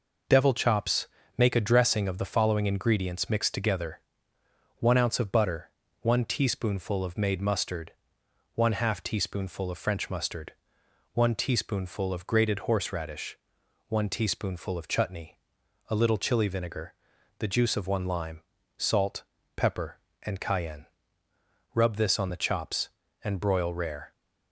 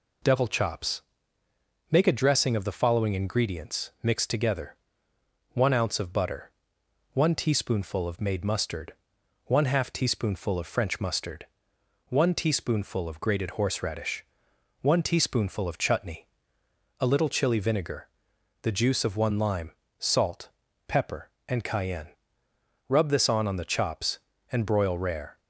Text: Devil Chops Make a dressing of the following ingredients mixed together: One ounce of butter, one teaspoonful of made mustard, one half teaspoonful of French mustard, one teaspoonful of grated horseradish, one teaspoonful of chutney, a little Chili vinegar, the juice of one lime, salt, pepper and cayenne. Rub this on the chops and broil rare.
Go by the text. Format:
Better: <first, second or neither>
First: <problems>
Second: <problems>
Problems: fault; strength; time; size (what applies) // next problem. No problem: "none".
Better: first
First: pauses between "Chops" and "Make"; slight; at 1.0 s; 0.32 s long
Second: pauses between "Chops" and "Make"; noticeable; at 1.0 s; 0.90 s long // says "on" twice; at 23.4 s